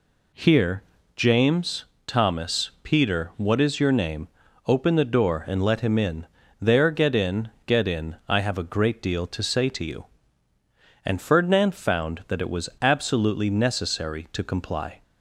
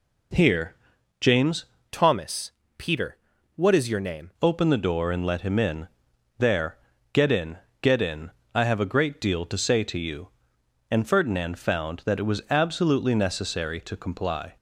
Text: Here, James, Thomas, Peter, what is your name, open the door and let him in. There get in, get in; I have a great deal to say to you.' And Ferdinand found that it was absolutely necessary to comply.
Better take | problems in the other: first | changes voice from "Thomas" to "name"; from 1.9 to 4.2 s; 2.3 s long // pauses between "There" and "get"; slight; at 6.7 s; 0.36 s long

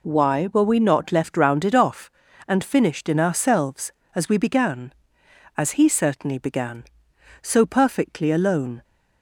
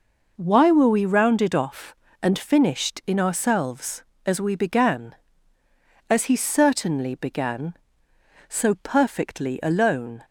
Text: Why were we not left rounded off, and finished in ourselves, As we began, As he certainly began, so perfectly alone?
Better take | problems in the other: first | skips "not left"; at 1.0 s

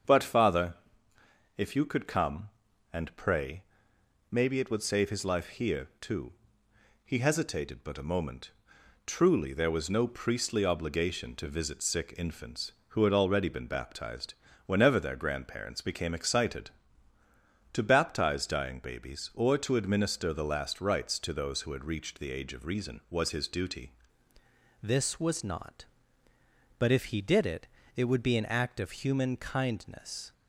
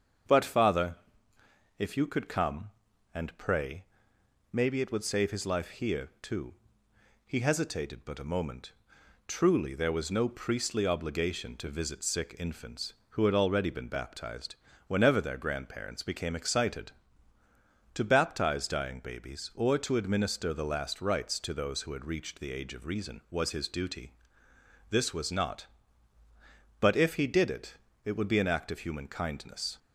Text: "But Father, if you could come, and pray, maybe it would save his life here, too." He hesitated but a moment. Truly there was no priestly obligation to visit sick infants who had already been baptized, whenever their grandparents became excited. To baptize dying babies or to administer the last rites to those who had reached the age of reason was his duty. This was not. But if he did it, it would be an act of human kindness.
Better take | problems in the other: second | starts louder than the rest; strong; until 1.8 s; 7 dB; strong in the second // changes voice at "This"; from 24.8 s on; 5.5 s long

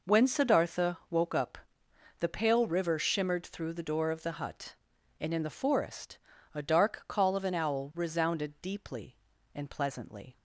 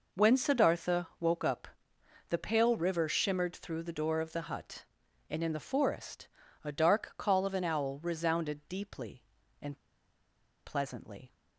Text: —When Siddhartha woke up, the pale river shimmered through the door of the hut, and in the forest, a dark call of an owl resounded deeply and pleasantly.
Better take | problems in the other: first | pauses between "and" and "pleasantly"; noticeable; at 9.7 s; 0.88 s long

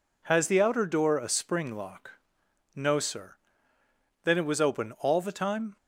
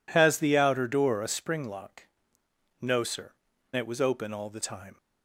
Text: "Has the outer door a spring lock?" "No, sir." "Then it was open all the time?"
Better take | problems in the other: first | skips "Then"; at 3.5 s

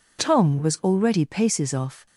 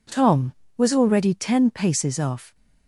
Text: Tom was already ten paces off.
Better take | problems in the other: second | skips "ten"; at 1.2 s

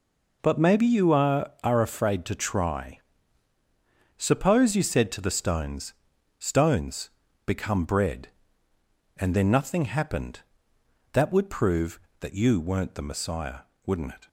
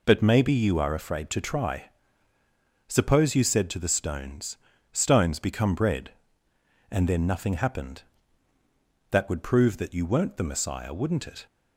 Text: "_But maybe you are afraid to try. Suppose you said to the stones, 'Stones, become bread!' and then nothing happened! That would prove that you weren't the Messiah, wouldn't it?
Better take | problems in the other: second | says "are" twice; at 1.6 s

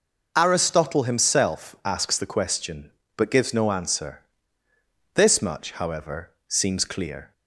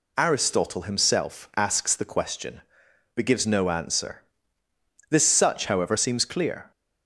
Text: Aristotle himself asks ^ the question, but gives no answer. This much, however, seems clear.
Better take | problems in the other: first | says "such" for "much"; at 5.2 s

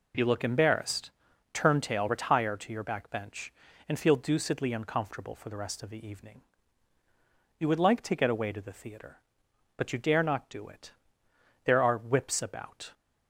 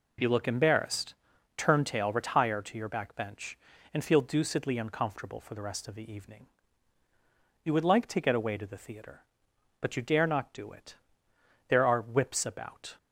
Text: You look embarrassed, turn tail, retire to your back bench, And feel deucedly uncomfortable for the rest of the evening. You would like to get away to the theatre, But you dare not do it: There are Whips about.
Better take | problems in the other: neither | none

